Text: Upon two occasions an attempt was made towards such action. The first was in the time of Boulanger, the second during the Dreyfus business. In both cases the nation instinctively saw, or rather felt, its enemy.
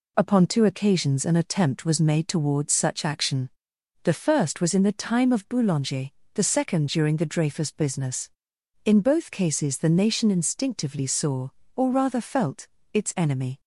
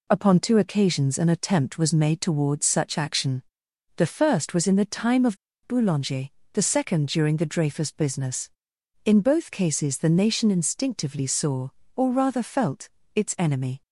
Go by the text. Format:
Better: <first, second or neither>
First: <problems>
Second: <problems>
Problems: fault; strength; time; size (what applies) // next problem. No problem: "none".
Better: first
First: none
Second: pauses between "of" and "Boulanger"; slight; at 5.3 s; 0.28 s long